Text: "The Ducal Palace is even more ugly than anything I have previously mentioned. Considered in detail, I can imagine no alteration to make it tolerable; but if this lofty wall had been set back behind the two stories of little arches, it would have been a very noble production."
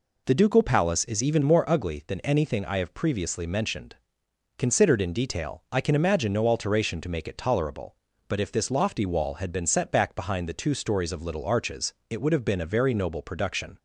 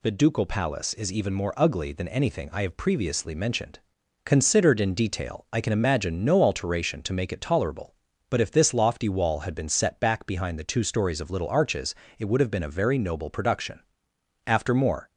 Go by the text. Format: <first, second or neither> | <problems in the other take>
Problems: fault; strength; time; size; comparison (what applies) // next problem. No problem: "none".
first | goes on to say "After more"; noticeable; from 14.4 s on; 0.64 s long